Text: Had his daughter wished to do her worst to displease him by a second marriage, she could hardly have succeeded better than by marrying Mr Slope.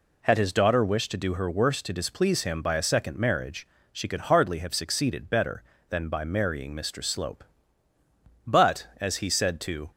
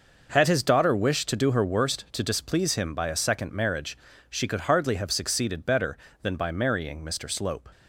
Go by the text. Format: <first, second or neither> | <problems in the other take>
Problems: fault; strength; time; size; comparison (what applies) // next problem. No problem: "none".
second | goes on to say "But as he said to"; from 8.4 s on; 1.4 s long